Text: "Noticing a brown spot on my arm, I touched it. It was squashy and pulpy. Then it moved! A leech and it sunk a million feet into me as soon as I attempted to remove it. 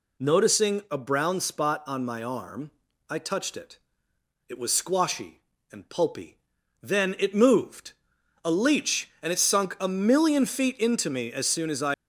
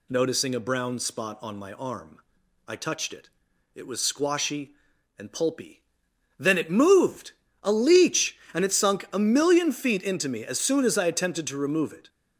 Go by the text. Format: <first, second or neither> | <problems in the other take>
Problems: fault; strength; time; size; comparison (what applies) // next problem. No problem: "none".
second | stops before "attempted to remove it"; at 11.9 s